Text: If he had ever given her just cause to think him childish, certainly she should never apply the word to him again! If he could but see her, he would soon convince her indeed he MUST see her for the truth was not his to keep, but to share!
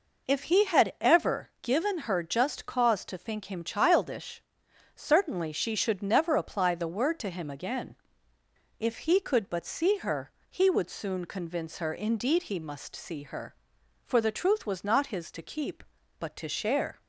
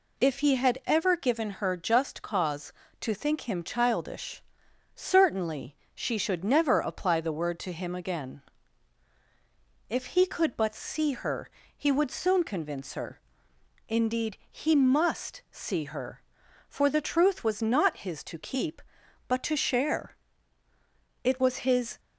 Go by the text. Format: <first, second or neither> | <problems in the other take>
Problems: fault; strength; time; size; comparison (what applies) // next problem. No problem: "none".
first | pauses between "certainly" and "she"; slight; at 5.7 s; 0.18 s long // pauses between "her" and "indeed"; noticeable; at 13.1 s; 0.68 s long // goes on to say "It was his"; noticeable; from 21.2 s on; 0.76 s long